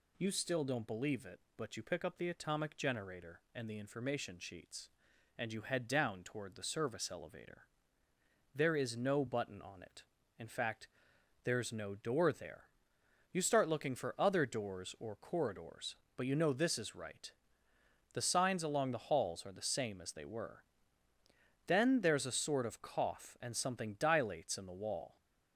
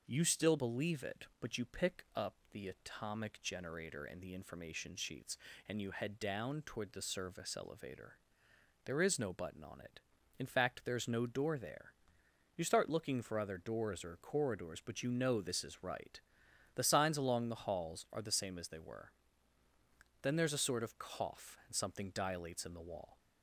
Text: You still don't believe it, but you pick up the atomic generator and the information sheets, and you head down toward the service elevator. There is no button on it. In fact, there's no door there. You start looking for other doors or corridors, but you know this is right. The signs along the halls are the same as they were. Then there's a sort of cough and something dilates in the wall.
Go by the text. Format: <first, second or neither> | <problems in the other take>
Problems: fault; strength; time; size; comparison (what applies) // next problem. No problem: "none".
first | skips "don't"; at 0.5 s // pauses between "up" and "the"; slight; at 2.3 s; 0.16 s long